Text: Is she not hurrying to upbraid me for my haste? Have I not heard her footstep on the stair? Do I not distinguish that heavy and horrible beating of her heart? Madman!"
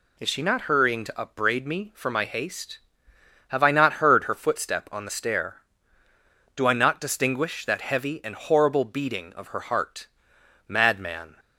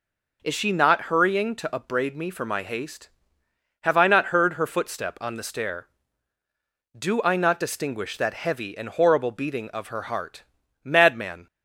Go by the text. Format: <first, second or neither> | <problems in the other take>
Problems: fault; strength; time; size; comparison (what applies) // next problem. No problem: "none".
neither | none